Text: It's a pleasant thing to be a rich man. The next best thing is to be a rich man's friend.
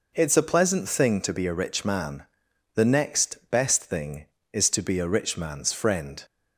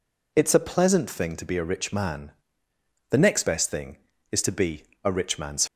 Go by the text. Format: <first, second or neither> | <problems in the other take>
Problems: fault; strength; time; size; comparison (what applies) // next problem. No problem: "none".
first | pauses between "be" and "a"; slight; at 4.8 s; 0.22 s long // stops before "friend"; at 5.6 s